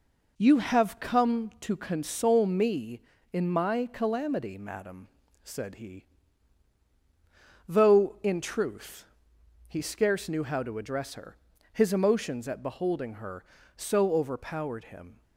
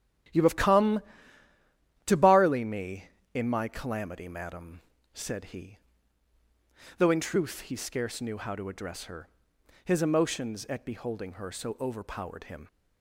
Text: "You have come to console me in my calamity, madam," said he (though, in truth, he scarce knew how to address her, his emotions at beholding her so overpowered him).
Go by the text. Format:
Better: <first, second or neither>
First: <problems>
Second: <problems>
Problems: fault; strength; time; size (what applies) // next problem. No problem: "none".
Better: first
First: none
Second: starts louder than the rest; strong; until 2.3 s; 12 dB // says "barley" for "console"; at 2.1 s